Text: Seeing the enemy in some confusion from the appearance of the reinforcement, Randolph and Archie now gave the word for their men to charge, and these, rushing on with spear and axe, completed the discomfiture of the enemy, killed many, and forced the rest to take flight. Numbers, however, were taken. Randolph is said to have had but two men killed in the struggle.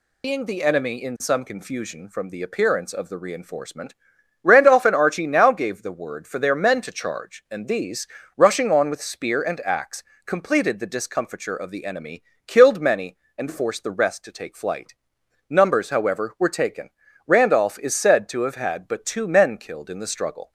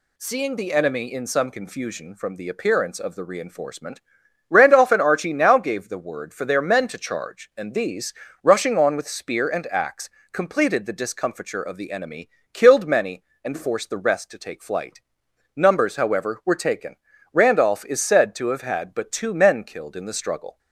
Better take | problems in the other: second | loses the start of "Seeing"; at 0.2 s; 180 ms

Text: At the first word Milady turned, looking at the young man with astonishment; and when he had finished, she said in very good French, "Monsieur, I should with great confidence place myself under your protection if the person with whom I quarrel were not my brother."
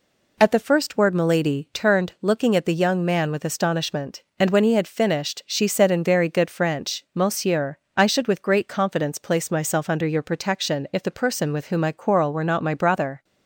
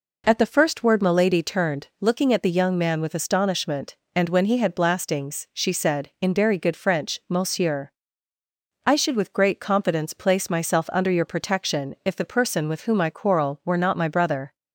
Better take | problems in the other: first | says "blastings" for "finished"; at 4.7 s

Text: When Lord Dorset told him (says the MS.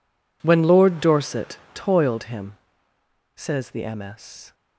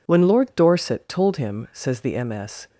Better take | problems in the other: second | says "toiled" for "told"; at 1.7 s

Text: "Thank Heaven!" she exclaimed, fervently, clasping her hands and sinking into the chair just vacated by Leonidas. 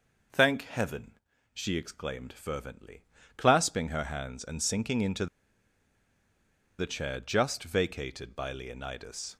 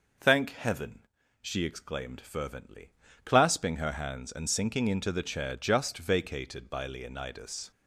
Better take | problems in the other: second | pauses between "into" and "the"; strong; at 5.2 s; 1.5 s long

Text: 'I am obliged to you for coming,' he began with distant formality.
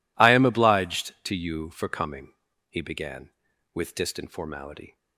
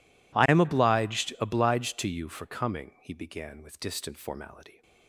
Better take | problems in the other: first | says "obliged" twice; at 1.3 s

